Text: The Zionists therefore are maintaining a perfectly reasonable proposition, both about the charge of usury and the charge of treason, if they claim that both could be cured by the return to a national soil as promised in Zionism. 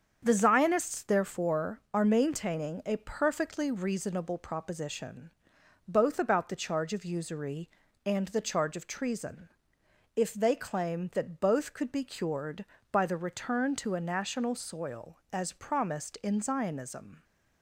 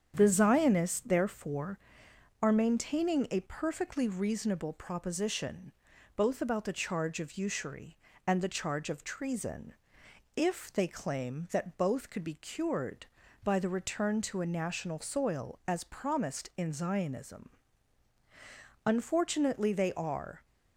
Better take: first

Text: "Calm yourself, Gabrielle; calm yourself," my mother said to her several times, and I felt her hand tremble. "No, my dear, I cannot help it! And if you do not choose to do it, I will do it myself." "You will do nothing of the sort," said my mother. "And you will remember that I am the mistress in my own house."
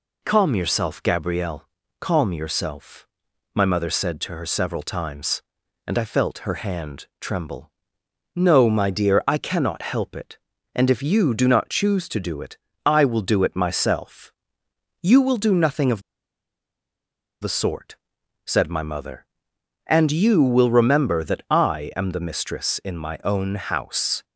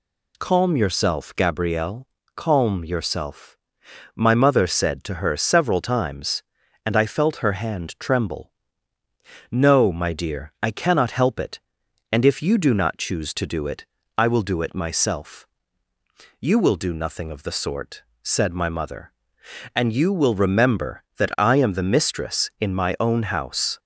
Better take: second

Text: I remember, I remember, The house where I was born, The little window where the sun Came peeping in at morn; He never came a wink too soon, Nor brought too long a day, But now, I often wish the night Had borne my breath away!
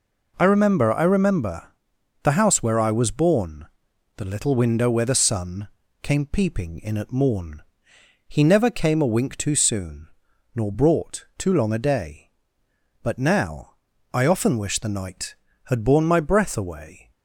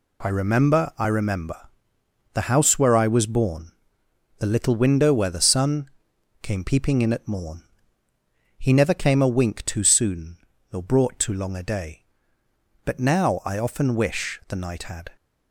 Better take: first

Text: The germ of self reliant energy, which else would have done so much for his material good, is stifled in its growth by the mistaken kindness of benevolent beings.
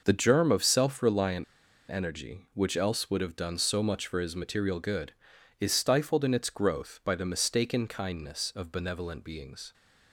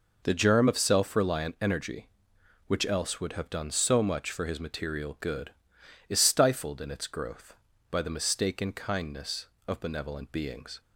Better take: second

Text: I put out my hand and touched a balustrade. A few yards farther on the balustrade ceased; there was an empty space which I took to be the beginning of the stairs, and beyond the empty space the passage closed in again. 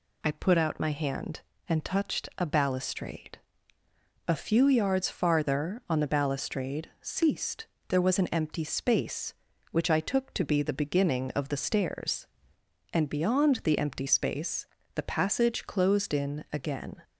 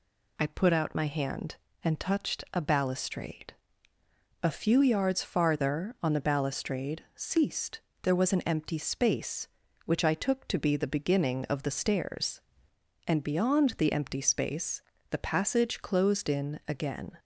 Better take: neither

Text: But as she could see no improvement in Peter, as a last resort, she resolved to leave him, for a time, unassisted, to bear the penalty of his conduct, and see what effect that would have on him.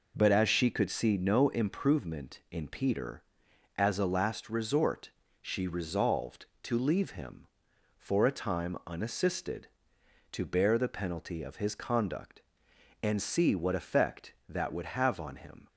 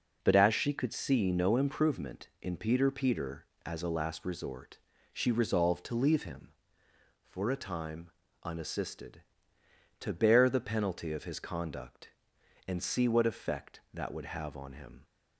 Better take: first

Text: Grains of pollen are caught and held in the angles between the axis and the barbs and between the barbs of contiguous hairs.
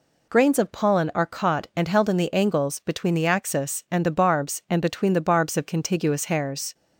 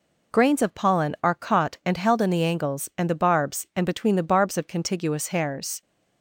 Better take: first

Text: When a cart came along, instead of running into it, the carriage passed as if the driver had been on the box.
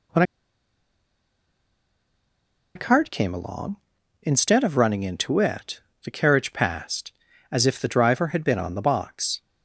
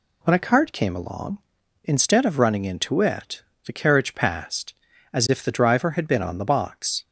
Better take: second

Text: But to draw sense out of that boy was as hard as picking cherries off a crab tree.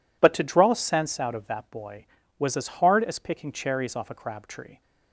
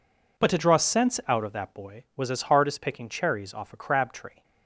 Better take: neither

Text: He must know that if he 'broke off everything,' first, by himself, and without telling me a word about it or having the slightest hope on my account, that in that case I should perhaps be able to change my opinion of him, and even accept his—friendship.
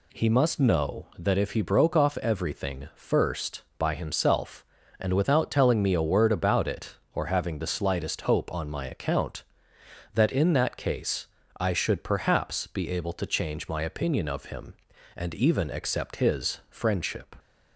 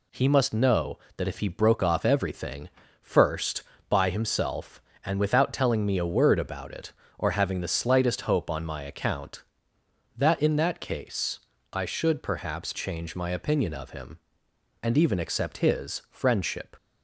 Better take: first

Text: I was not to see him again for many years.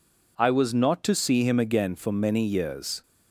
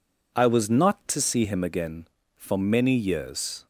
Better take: neither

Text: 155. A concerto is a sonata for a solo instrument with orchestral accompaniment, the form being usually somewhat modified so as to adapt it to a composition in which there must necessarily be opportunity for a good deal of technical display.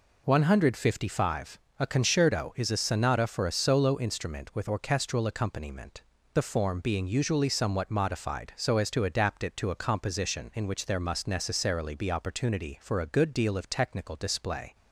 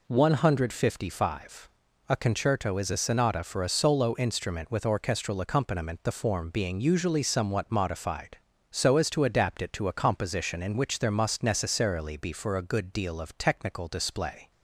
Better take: first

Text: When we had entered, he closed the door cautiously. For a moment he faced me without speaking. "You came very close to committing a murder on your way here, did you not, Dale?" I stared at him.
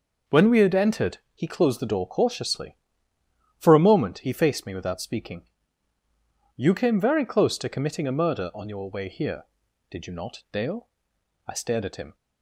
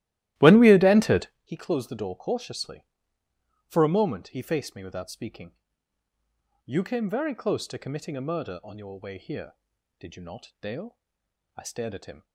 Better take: first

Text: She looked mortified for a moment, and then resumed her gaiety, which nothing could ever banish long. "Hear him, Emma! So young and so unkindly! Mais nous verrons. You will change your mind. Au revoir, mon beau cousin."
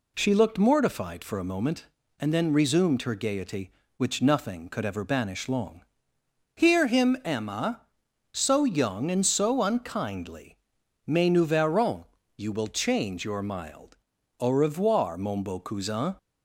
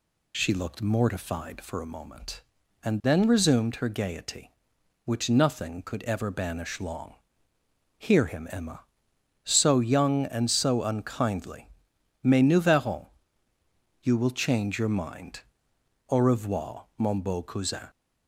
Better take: second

